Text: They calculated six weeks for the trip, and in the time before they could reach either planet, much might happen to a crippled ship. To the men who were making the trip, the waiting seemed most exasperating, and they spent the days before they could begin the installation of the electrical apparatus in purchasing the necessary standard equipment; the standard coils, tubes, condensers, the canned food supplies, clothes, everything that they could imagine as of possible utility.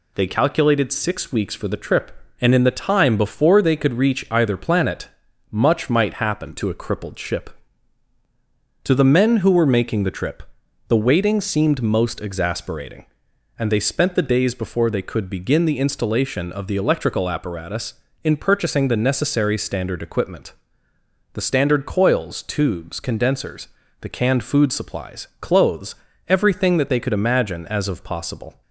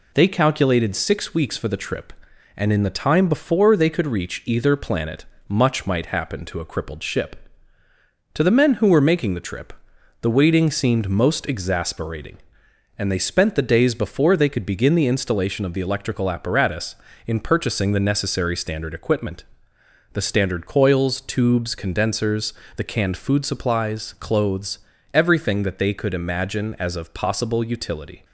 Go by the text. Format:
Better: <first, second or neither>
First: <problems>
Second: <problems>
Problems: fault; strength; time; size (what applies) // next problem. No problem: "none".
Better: second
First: stops before "utility"; at 28.6 s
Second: none